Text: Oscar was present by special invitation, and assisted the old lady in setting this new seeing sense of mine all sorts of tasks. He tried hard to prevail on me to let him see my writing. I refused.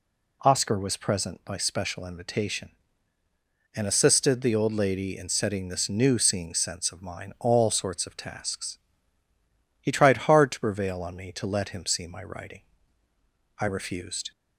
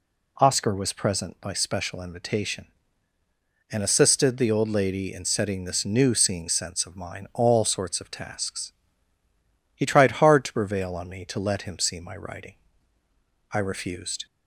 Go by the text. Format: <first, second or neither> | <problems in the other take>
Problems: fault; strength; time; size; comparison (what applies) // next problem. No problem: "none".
neither | none